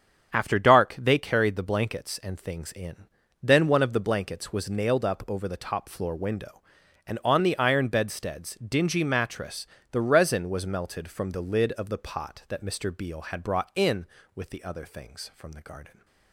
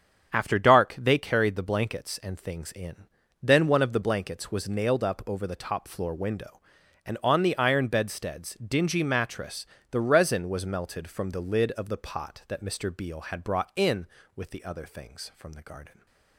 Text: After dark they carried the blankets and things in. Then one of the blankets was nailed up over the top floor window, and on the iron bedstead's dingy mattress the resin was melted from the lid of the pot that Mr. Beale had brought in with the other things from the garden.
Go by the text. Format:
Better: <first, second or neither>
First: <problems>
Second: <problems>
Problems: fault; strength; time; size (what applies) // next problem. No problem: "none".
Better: neither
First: starts louder than the rest; strong; until 1.3 s; 7.5 dB // pauses between "mattress" and "the"; slight; at 9.6 s; 0.26 s long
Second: starts louder than the rest; strong; until 1.3 s; 7.5 dB // pauses between "mattress" and "the"; slight; at 9.6 s; 0.26 s long